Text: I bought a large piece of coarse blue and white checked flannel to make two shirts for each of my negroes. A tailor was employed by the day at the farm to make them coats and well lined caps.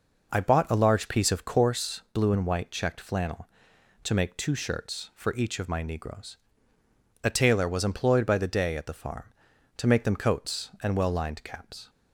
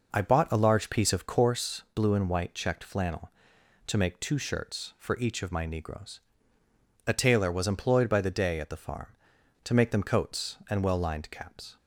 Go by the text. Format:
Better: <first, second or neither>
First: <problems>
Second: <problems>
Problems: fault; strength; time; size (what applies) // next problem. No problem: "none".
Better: neither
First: none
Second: none